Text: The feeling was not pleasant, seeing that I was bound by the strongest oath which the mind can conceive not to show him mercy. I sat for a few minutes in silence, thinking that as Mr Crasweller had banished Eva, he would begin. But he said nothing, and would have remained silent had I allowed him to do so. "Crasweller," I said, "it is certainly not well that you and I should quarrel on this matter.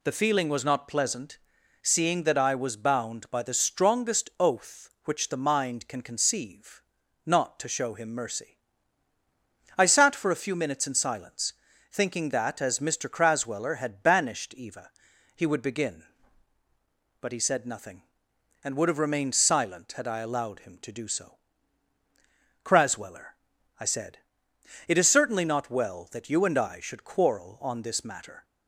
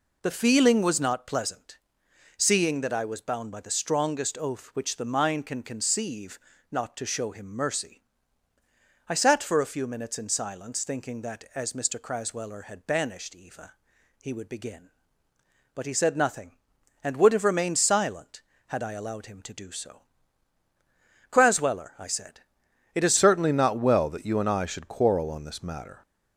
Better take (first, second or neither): first